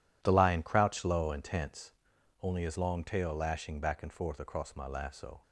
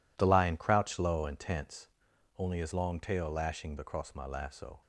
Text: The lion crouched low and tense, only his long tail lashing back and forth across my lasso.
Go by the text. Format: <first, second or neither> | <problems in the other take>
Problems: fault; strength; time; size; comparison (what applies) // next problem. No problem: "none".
first | skips "back and forth"; at 3.7 s